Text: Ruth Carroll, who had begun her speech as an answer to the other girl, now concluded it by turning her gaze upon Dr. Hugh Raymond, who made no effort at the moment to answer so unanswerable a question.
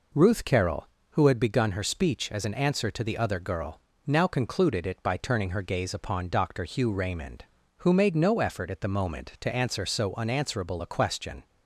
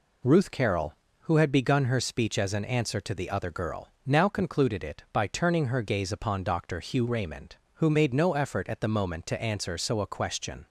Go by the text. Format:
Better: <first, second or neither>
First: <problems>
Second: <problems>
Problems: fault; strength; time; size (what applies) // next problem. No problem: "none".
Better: first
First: none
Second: skips "unanswerable"; at 10.0 s